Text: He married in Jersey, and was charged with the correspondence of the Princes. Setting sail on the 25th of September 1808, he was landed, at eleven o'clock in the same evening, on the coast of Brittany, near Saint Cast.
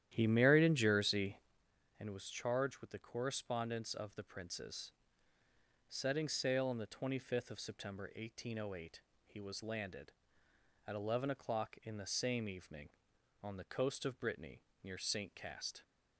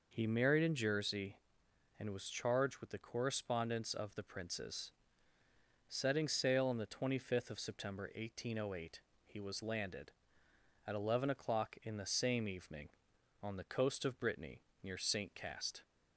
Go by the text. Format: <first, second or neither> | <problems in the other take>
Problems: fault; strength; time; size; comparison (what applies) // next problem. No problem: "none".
second | starts louder than the rest; strong; until 1.6 s; 11.5 dB